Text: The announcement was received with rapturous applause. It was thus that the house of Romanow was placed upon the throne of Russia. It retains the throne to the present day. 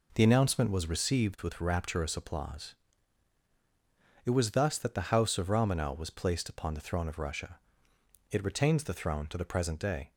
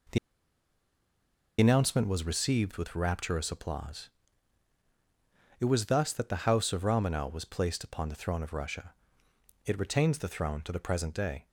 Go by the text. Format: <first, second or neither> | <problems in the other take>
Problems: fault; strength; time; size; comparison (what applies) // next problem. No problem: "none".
first | pauses between "The" and "announcement"; strong; at 0.1 s; 1.4 s long